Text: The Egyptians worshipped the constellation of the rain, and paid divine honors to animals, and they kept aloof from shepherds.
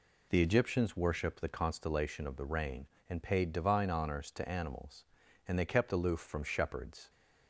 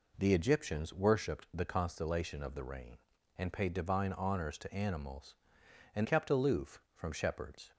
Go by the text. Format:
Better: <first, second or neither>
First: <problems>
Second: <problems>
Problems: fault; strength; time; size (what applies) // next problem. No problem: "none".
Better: first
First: none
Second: skips "they"; at 6.0 s